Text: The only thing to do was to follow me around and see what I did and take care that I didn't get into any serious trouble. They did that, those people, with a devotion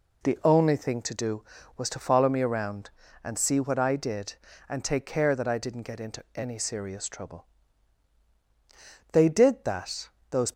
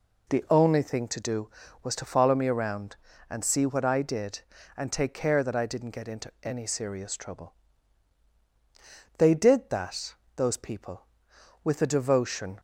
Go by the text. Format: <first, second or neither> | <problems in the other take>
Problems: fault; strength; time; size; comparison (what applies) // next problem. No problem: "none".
second | stops before "people with a devotion"; at 10.5 s